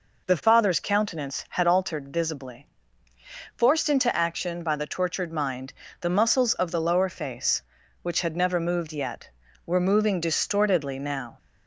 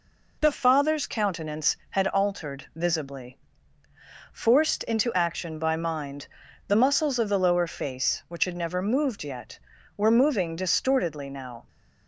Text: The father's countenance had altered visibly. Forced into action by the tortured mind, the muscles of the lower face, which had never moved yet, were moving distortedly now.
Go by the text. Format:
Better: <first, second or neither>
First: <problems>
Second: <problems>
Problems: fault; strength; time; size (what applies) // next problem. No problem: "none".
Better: first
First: none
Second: skips "the tortured"; at 5.7 s